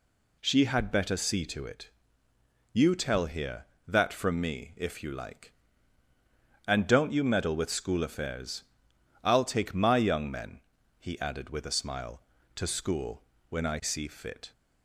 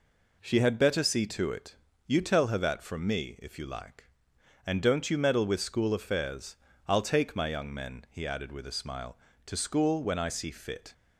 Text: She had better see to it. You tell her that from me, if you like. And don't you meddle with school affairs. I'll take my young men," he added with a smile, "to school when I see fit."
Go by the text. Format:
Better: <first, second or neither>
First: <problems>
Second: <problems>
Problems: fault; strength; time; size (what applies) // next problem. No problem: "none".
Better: second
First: says "here" for "her"; at 3.2 s // pauses between "school" and "when"; slight; at 13.2 s; 0.24 s long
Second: none